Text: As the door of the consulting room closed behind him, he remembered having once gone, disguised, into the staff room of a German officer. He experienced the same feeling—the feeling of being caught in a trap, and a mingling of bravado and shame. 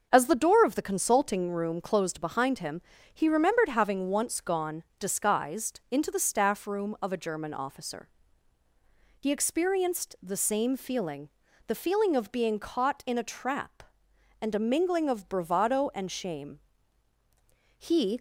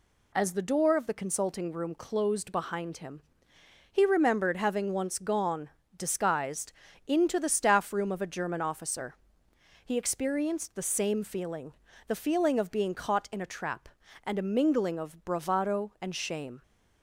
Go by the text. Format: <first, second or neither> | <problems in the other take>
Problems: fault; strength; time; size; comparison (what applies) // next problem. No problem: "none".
second | goes on to say "He"; slight; from 17.7 s on; 0.42 s long